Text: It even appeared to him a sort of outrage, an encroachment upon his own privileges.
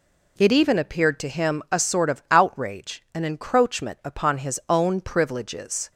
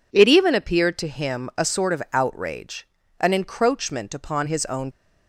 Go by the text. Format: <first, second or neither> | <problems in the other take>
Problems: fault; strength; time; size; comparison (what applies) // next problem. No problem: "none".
first | stops before "privileges"; at 4.9 s